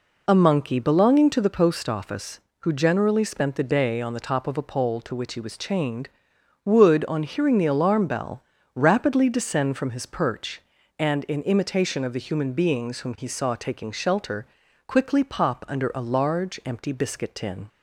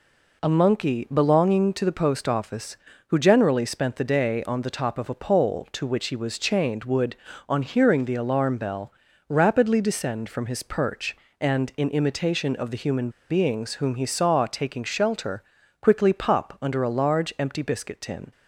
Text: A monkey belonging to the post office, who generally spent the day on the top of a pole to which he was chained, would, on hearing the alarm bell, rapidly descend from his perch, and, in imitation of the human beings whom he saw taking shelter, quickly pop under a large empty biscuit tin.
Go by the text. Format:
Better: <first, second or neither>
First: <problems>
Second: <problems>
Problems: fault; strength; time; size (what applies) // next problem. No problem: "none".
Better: first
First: none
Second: pauses between "human" and "beings"; slight; at 13.0 s; 0.20 s long